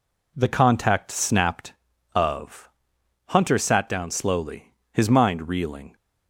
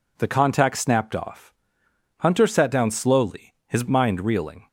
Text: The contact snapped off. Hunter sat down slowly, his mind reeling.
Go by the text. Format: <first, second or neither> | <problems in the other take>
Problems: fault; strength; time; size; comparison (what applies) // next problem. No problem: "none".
second | says "of" for "off"; at 2.1 s